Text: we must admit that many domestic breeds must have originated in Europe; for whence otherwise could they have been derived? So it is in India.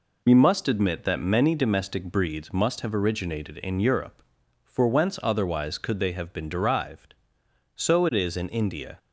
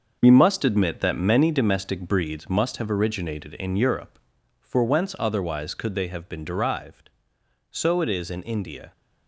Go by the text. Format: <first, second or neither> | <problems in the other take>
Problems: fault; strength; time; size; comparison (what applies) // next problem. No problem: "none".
first | gets quieter; strong; throughout; 9 dB